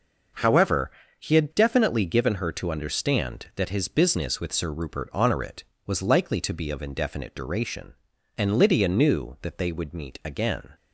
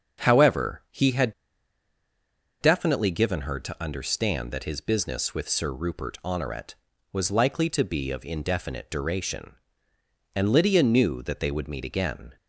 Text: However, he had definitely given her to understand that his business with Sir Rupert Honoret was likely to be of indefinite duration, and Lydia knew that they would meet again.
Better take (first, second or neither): first